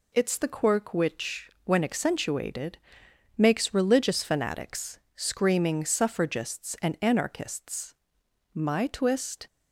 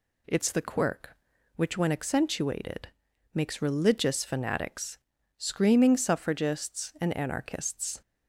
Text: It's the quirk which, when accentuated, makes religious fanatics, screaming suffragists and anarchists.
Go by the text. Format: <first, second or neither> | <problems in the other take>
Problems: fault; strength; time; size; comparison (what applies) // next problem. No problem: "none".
second | goes on to say "My twist"; noticeable; from 8.5 s on; 0.94 s long